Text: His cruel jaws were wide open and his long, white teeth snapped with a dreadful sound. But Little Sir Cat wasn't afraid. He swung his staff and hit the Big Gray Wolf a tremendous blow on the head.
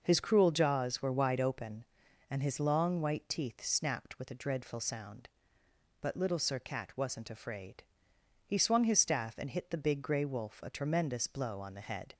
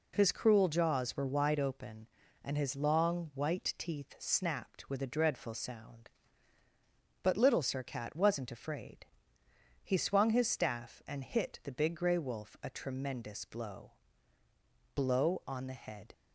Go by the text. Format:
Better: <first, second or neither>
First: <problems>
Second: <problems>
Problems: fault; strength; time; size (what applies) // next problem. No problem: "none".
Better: first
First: none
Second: says "blow" twice; at 14.9 s